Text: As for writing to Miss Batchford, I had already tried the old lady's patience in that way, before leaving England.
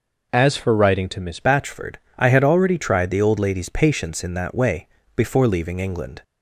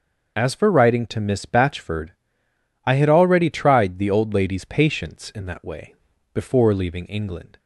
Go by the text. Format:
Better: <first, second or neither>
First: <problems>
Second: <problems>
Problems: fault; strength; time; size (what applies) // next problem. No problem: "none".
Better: second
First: changes voice at "Batchford"; from 1.4 s on; 4.8 s long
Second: none